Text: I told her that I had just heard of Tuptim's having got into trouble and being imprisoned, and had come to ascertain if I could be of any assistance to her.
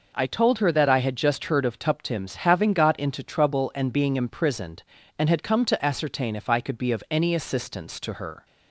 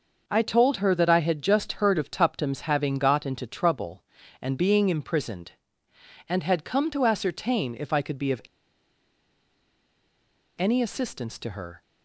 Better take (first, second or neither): first